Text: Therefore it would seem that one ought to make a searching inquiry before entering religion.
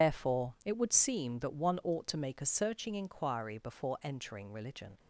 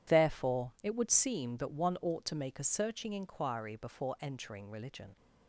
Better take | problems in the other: second | loses the start of "Therefore"; at 0.0 s; 110 ms

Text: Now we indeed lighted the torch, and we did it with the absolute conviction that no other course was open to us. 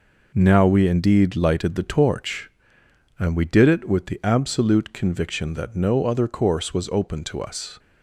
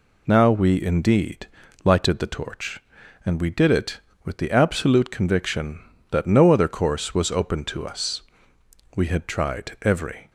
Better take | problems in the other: first | pauses between "indeed" and "lighted"; at 1.4 s; 0.38 s long // goes on to say "We had tried every"; from 8.9 s on; 1.3 s long

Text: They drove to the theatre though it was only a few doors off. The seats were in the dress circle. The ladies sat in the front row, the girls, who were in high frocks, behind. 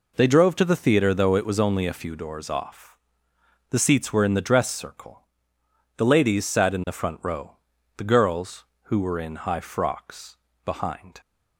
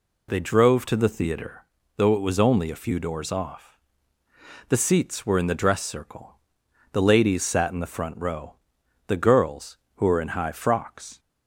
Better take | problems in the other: first | pauses between "theatre" and "though"; slight; at 1.6 s; 0.32 s long // stops before "behind"; at 11.1 s

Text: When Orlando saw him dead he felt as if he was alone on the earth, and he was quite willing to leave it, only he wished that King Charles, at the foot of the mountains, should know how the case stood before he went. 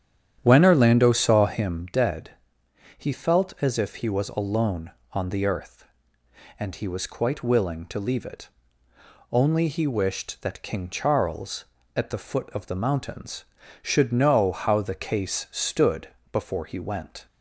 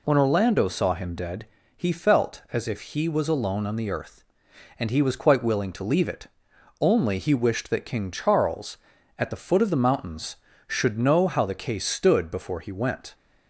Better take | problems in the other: second | starts louder than the rest; strong; until 1.8 s; 9.5 dB // pauses between "dead" and "he"; noticeable; at 2.3 s; 0.66 s long; slight in the second // pauses between "stood" and "before"; slight; at 16.0 s; 0.24 s long

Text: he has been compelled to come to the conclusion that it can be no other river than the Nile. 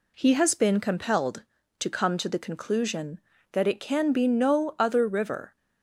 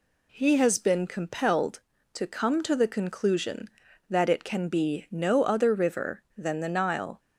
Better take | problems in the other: second | stops before "than the Nile"; at 5.5 s

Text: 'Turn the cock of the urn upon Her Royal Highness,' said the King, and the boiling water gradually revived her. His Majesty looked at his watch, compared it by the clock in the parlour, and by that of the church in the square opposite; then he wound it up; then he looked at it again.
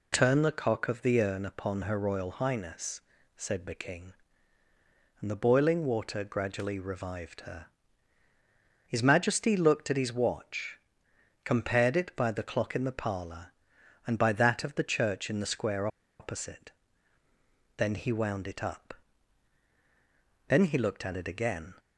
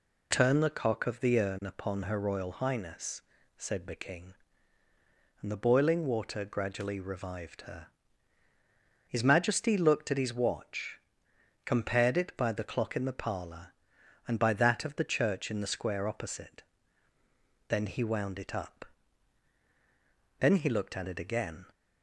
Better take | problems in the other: second | pauses between "square" and "opposite"; slight; at 15.8 s; 0.32 s long

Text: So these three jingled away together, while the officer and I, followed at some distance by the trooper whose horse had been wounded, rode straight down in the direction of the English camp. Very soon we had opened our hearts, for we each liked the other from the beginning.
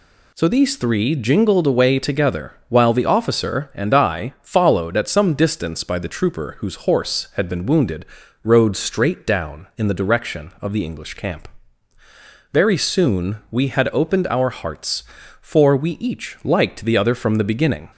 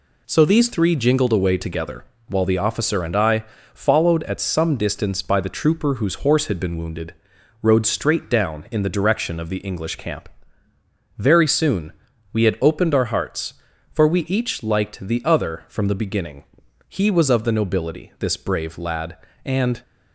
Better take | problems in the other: first | pauses between "soon" and "we"; at 11.9 s; 0.40 s long // goes on to say "He was of the nobility this brave lad and"; strong; from 16.8 s on; 2.9 s long

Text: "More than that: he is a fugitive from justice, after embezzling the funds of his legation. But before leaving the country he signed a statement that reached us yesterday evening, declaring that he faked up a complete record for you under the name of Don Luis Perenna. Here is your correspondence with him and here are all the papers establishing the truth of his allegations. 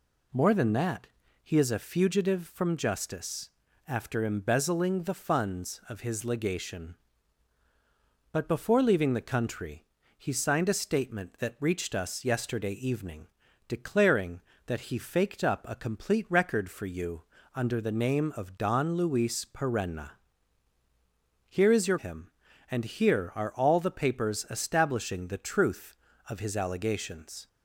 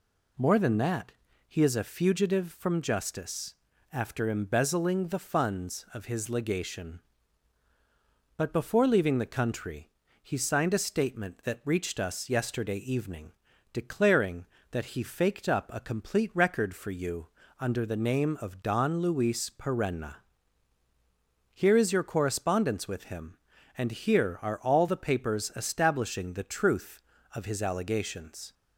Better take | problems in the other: second | pauses between "country" and "he"; slight; at 9.8 s; 0.30 s long; slight in the second // pauses between "you" and "under"; slight; at 17.2 s; 0.32 s long; slight in the second // skips "correspondence with"; at 21.9 s

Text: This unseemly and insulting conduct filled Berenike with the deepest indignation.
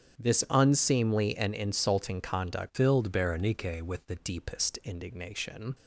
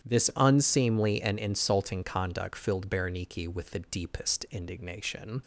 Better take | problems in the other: second | starts louder than the rest; strong; until 1.2 s; 9 dB; strong in the second // changes voice from "filled" to "the"; from 2.7 to 4.1 s; 1.4 s long

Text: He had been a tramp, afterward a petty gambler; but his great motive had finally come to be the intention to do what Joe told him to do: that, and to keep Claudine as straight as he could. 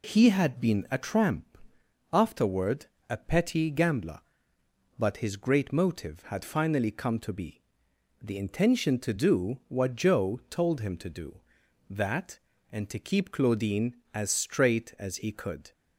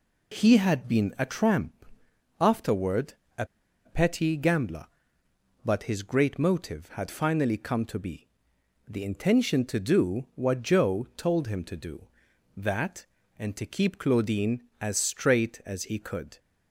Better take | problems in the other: first | pauses between "afterward" and "a"; slight; at 3.1 s; 0.24 s long; slight in the first // pauses between "a" and "petty"; at 3.4 s; 0.40 s long // pauses between "be" and "the"; noticeable; at 8.2 s; 0.60 s long; noticeable in the first

